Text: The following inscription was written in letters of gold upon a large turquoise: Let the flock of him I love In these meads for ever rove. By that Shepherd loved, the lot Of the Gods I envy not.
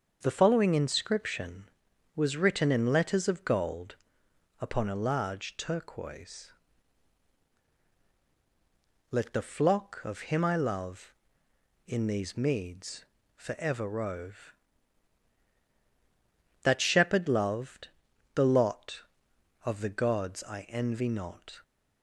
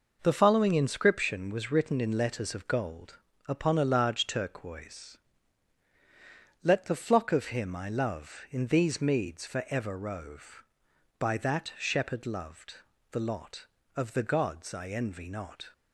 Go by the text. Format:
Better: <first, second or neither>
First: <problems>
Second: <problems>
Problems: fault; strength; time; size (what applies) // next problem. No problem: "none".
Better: second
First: starts louder than the rest; until 1.2 s; 6.5 dB // pauses between "gold" and "upon"; noticeable; at 3.9 s; 0.66 s long // skips "By"; at 15.5 s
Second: pauses between "gold" and "upon"; slight; at 3.1 s; 0.28 s long